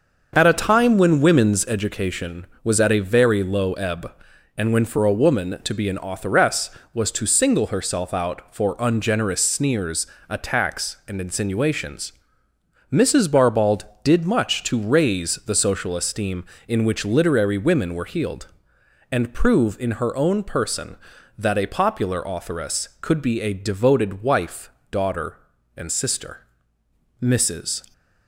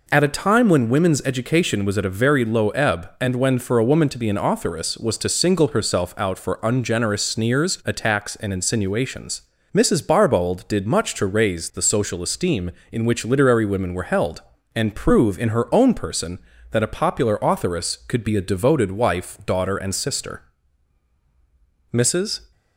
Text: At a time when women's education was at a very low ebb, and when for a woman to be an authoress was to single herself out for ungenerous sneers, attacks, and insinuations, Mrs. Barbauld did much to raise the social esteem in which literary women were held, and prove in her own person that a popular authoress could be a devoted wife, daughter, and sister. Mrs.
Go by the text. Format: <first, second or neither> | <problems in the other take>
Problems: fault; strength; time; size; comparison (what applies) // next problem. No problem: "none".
second | starts louder than the rest; until 1.3 s; 6 dB // says "healed" for "held"; at 18.0 s